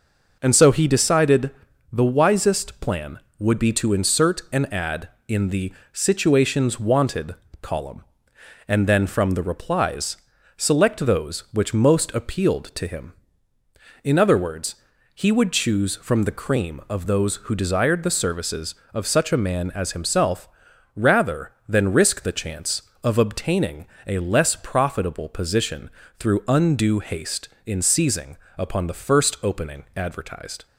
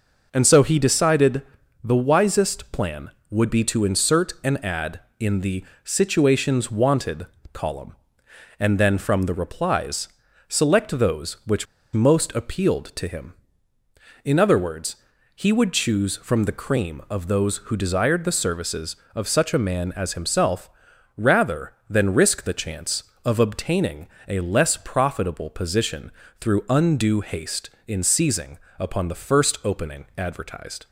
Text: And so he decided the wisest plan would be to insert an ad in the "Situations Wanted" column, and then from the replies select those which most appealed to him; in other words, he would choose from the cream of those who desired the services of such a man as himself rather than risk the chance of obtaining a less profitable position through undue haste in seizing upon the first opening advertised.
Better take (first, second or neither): first